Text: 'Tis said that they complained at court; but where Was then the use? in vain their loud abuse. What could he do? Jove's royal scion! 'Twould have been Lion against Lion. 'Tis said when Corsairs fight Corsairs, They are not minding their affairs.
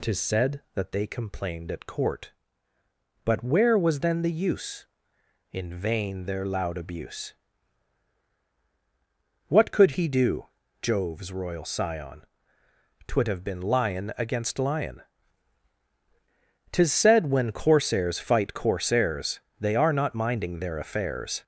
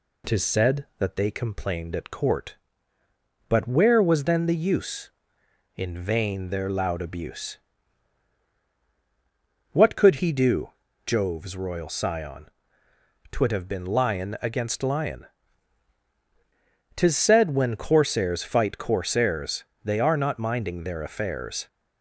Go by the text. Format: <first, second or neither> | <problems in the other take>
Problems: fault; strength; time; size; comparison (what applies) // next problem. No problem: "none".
second | gets louder; throughout; 7 dB